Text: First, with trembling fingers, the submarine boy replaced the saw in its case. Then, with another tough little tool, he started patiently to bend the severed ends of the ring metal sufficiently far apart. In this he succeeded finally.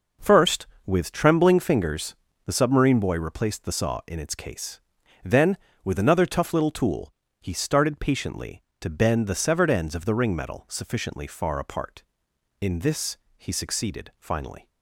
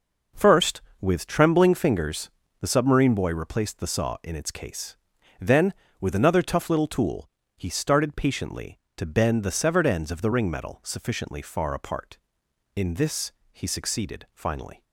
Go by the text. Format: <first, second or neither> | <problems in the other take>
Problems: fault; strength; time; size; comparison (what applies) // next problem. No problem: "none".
neither | pauses between "this" and "he"; slight; the same in both